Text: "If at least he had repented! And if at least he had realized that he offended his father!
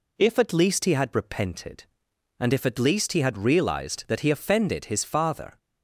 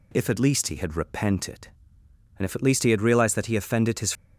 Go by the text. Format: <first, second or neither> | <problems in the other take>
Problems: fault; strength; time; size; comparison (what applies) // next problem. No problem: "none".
first | stops before "father"; at 4.1 s